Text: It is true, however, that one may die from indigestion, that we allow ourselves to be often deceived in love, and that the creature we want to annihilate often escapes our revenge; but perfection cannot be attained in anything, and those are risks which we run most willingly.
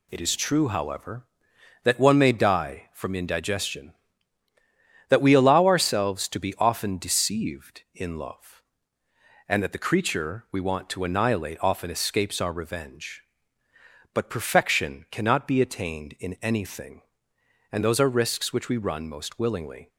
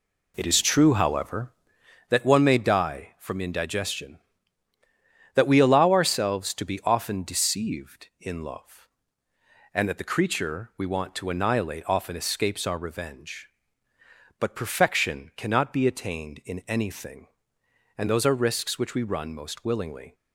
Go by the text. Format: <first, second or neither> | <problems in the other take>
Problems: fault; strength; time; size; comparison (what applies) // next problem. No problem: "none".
first | starts louder than the rest; slight; until 1.8 s; 2.5 dB